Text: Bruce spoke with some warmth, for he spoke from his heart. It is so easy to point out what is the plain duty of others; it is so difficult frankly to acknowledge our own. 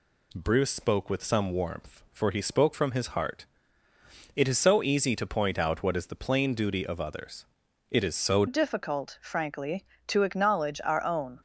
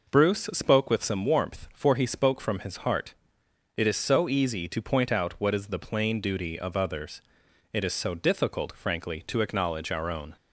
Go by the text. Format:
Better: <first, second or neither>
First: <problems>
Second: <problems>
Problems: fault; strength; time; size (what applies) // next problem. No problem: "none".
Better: second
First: changes voice at "difficult"; from 8.4 s on; 2.9 s long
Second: none